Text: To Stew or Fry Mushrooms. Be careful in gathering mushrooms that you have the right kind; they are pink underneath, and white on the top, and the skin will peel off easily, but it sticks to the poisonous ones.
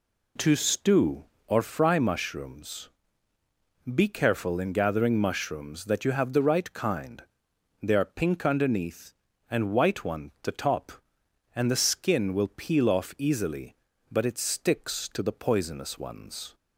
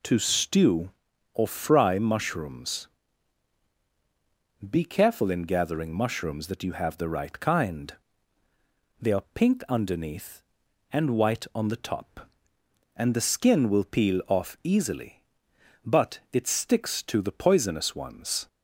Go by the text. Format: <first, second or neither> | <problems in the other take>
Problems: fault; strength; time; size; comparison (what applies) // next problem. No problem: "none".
second | says "one" for "on"; at 10.0 s